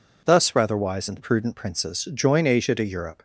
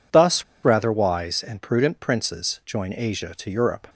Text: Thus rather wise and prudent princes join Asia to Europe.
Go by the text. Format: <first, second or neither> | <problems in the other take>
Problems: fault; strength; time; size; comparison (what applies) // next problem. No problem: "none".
first | pauses between "Thus" and "rather"; slight; at 0.4 s; 0.19 s long